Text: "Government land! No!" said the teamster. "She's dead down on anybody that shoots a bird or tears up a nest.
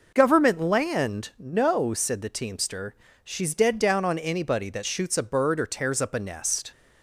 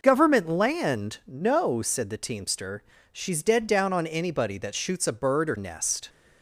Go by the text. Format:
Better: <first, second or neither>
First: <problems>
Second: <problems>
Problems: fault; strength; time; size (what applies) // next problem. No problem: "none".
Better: first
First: none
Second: skips "tears up a"; at 5.5 s